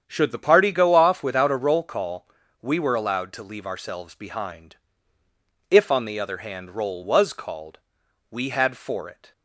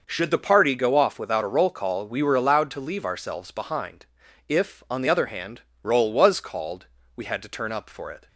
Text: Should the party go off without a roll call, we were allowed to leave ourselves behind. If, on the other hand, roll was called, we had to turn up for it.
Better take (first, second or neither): second